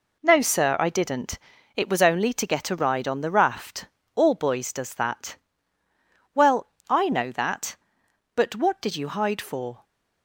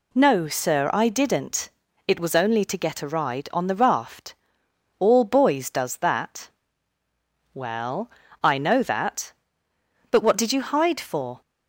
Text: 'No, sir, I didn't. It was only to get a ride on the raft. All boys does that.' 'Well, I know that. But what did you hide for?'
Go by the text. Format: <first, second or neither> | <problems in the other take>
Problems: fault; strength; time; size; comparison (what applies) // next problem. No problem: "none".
second | gets quieter; throughout; 7 dB